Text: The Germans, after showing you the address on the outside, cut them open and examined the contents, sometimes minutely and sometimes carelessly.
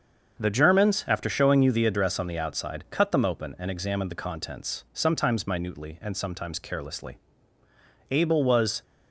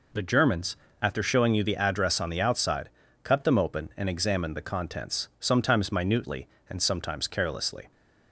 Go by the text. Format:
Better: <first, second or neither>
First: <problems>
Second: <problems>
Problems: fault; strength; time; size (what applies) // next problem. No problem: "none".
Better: second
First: starts louder than the rest; until 1.4 s; 6.5 dB // goes on to say "Abel was"; noticeable; from 8.0 s on; 0.72 s long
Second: none